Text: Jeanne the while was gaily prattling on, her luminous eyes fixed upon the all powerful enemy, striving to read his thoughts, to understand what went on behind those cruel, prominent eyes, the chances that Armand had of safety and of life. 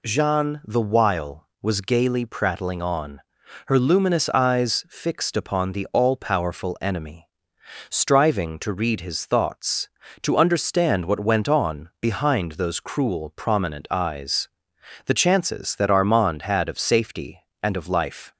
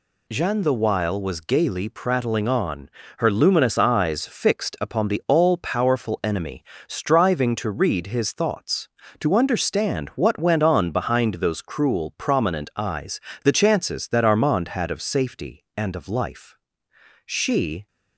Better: first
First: none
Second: goes on to say "She"; noticeable; from 17.2 s on; 0.62 s long

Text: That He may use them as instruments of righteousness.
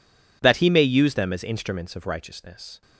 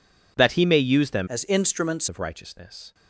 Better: first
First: none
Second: changes voice from "as" to "instruments"; from 1.2 to 2.0 s; 0.8 s long

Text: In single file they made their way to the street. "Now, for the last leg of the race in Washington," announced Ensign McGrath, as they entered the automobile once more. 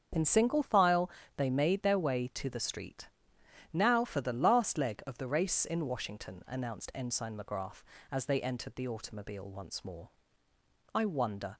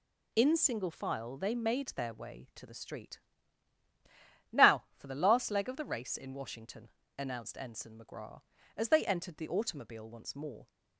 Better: second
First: starts louder than the rest; strong; until 1.4 s; 7 dB // pauses between "file" and "they"; slight; at 1.0 s; 0.28 s long // goes on to say "I wonder"; noticeable; from 10.9 s on; 0.64 s long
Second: none

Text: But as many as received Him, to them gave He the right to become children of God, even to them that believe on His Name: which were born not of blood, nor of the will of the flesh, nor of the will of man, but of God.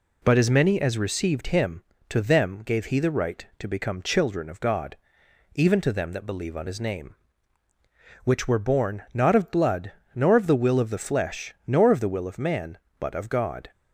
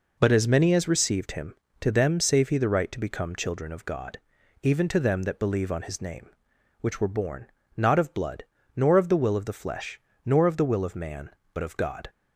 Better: first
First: none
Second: says "save" for "gave"; at 2.1 s // pauses between "born" and "not"; slight; at 7.4 s; 0.30 s long

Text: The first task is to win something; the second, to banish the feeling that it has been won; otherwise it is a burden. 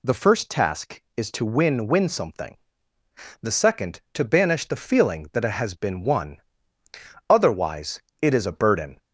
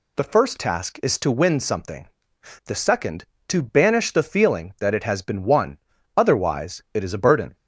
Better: second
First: says "win" twice; at 1.8 s // pauses between "otherwise" and "it"; slight; at 7.9 s; 0.22 s long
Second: none

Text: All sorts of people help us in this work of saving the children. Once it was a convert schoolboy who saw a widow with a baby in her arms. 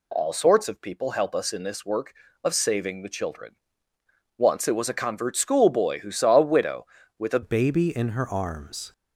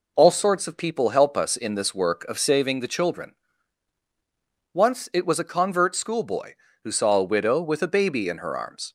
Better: second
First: changes voice at "baby"; from 7.4 s on; 1.5 s long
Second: none

